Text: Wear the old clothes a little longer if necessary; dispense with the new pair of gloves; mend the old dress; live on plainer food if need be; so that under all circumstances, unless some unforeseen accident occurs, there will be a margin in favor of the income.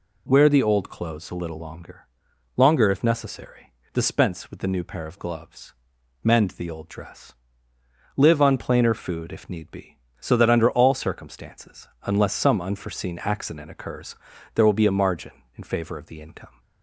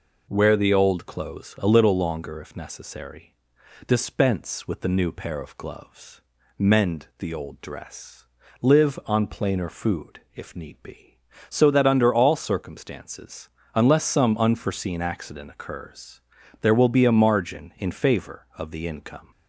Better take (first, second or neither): second